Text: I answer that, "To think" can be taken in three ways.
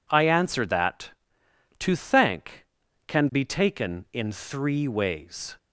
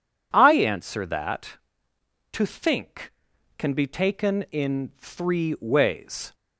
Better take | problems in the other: second | says "thank" for "think"; at 1.9 s

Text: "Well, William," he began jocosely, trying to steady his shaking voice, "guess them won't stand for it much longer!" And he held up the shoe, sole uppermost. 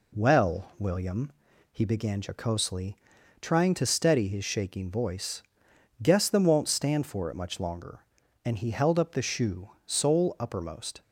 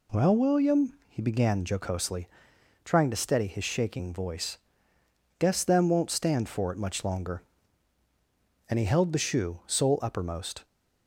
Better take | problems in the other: first | skips "up"; at 9.1 s

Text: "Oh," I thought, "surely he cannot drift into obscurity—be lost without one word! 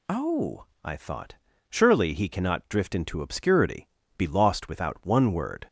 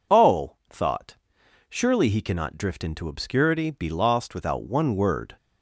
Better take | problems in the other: first | skips "I"; at 0.6 s

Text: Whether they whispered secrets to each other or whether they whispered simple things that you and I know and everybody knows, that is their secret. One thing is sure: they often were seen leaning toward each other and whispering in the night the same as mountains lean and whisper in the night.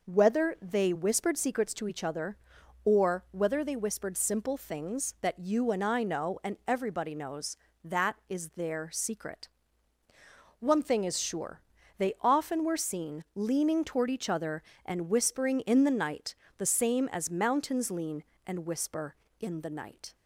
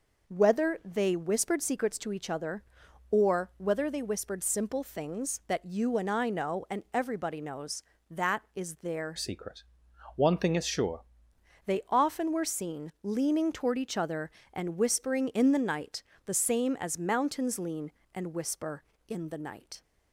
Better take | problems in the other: first | changes voice from "secret" to "sure"; from 9.1 to 11.0 s; 1.9 s long // pauses between "night" and "the"; slight; at 16.0 s; 0.22 s long; slight in the first

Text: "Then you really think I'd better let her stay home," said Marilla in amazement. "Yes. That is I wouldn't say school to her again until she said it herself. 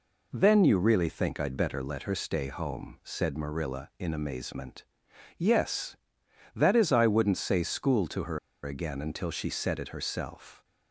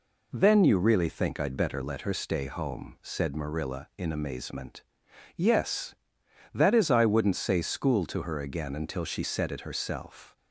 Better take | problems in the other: second | pauses between "her" and "again"; slight; at 8.3 s; 0.27 s long

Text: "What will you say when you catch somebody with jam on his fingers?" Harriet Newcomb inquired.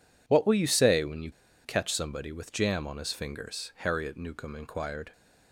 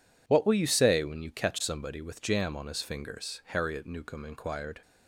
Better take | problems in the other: second | pauses between "you" and "catch"; slight; at 1.3 s; 0.34 s long

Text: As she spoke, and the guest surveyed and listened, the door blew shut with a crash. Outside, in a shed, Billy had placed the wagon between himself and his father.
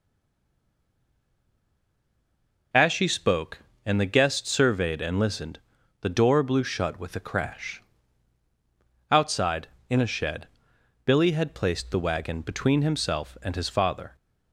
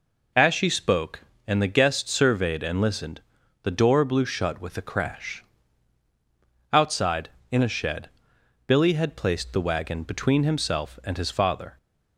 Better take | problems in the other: second | stays silent before the first word; strong; until 2.7 s; 2.7 s long

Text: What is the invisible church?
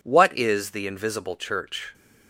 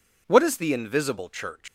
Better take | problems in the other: neither | none

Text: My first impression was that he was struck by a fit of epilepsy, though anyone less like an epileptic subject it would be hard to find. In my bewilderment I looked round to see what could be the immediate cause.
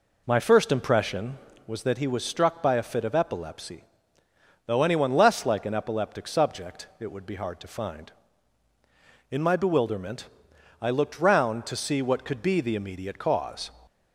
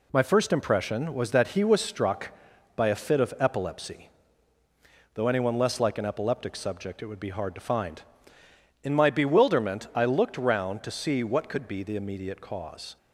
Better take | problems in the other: second | starts louder than the rest; until 1.5 s; 4 dB // pauses between "bewilderment" and "I"; noticeable; at 10.2 s; 0.54 s long

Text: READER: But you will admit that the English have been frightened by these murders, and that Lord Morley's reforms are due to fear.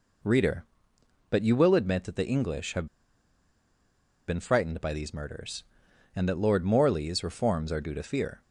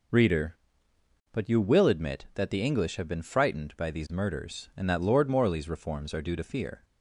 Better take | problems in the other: second | pauses between "have" and "been"; strong; at 2.8 s; 1.4 s long

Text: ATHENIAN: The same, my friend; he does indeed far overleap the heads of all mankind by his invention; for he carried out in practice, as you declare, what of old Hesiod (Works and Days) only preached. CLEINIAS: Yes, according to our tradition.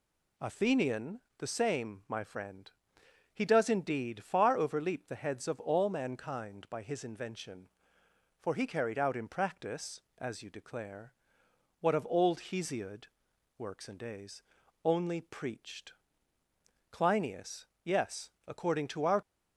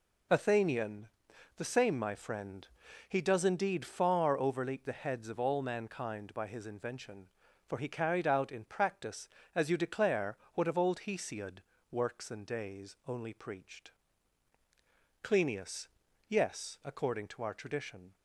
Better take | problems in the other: second | stops before "tradition"; at 19.2 s

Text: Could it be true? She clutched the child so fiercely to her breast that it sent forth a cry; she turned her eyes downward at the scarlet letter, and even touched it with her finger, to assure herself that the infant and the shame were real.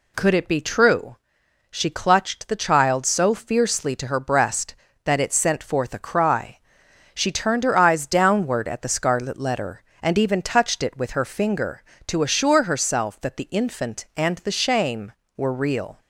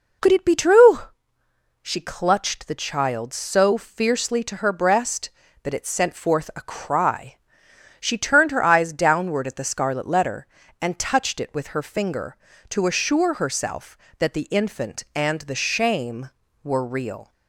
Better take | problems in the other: first | skips "even"; at 10.9 s

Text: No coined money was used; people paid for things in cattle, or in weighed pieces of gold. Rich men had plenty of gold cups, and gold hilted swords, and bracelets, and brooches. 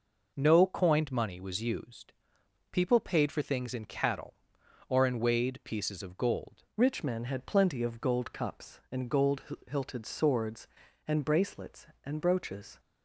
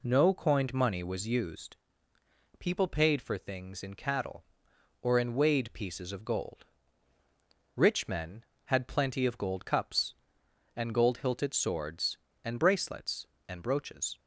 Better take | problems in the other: second | changes voice at "Rich"; from 6.7 s on; 6.0 s long // pauses between "gold" and "hilted"; slight; at 9.4 s; 0.26 s long

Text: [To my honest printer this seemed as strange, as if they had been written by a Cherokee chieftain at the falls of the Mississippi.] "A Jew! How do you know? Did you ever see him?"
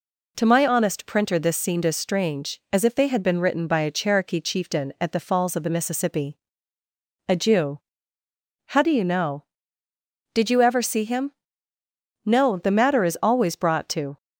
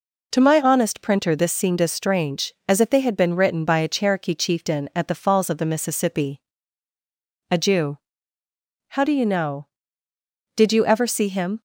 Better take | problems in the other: second | goes on to say "No the matter is always brought to"; strong; from 12.2 s on; 1.9 s long

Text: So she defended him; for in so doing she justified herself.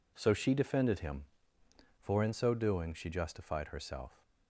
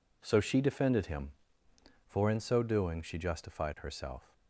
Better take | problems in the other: neither | none

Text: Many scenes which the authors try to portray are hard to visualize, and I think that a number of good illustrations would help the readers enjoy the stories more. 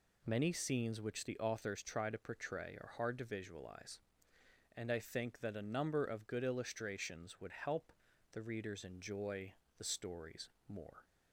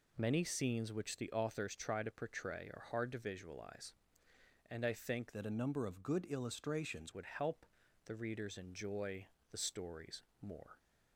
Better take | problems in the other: first | changes voice from "that" to "illustrations"; from 5.3 to 7.1 s; 1.8 s long // pauses between "help" and "the"; at 7.6 s; 0.38 s long; also in the first // pauses between "enjoy" and "the"; slight; at 9.2 s; 0.24 s long; slight in the first // pauses between "stories" and "more"; slight; at 10.2 s; 0.20 s long; slight in the first

